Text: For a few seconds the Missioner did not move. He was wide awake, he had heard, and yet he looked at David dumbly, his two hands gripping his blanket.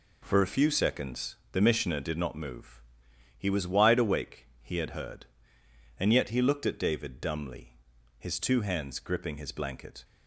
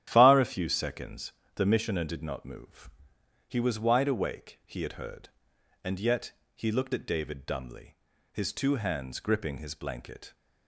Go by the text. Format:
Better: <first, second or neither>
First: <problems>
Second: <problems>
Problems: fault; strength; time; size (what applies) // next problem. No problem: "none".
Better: first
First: pauses between "seconds" and "the"; slight; at 1.3 s; 0.16 s long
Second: starts louder than the rest; strong; until 1.1 s; 11.5 dB // says "Far" for "For"; at 0.1 s // pauses between "seconds" and "the"; slight; at 1.3 s; 0.22 s long // pauses between "yet" and "he"; slight; at 6.3 s; 0.24 s long